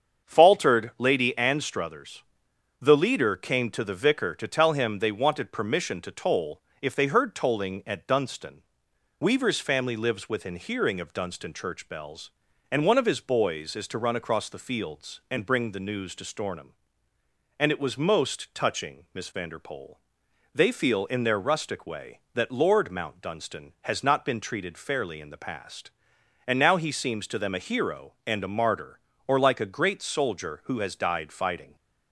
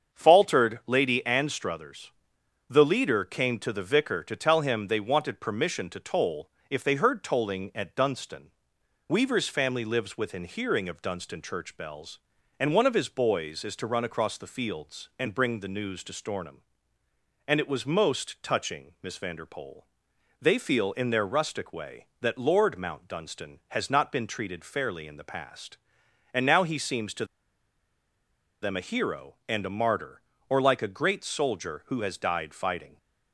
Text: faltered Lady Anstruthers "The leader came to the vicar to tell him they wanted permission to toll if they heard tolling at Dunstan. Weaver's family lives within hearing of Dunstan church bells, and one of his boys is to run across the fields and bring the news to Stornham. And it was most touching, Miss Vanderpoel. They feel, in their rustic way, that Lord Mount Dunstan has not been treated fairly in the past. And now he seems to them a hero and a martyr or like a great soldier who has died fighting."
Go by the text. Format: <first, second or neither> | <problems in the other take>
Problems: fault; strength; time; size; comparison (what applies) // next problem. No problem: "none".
first | starts louder than the rest; strong; until 1.2 s; 7 dB; strong in the first // pauses between "Anstruthers" and "The"; noticeable; at 2.1 s; 0.56 s long; noticeable in the first // pauses between "toll" and "if"; slight; at 6.4 s; 0.20 s long; slight in the first // pauses between "to" and "them"; strong; at 27.2 s; 1.3 s long